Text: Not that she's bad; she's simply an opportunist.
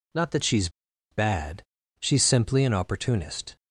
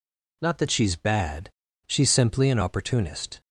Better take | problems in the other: second | pauses between "she's" and "bad"; at 0.6 s; 0.41 s long

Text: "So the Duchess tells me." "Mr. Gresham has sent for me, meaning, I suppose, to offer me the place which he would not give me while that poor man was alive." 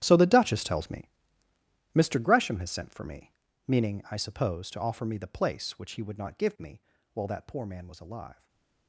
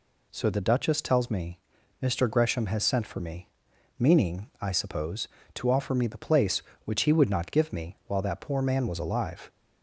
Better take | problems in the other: second | gets quieter; strong; throughout; 17 dB // pauses between "me" and "while"; slight; at 6.7 s; 0.36 s long // stays silent after the last word; slight; from 8.3 s on; 0.5 s long

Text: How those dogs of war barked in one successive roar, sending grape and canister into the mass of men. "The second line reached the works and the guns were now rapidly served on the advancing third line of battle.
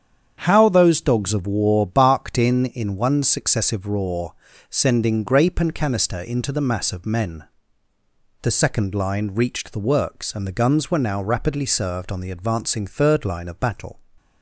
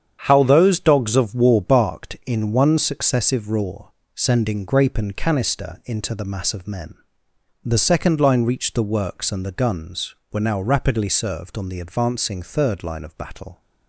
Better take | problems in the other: second | starts louder than the rest; strong; until 1.4 s; 8 dB; strong in the second // says "in" twice; at 2.6 s

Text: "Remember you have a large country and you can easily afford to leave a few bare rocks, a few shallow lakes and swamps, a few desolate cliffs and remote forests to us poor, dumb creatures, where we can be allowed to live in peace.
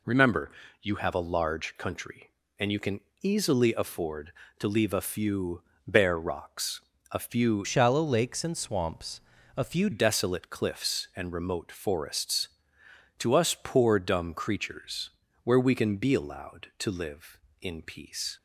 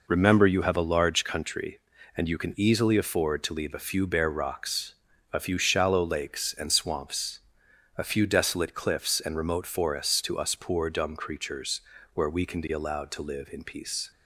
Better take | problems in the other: second | pauses between "Remember" and "you"; slight; at 0.5 s; 0.32 s long // pauses between "can" and "easily"; slight; at 3.0 s; 0.22 s long // pauses between "few" and "bare"; slight; at 5.6 s; 0.24 s long // changes voice from "shallow" to "few"; from 7.6 to 9.8 s; 2.2 s long

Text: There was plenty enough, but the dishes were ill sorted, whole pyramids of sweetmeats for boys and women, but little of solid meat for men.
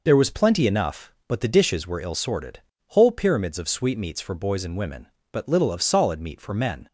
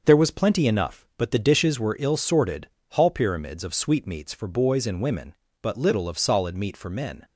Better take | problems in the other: first | starts louder than the rest; noticeable; until 1.0 s; 6 dB // says "hall" for "whole"; at 2.8 s

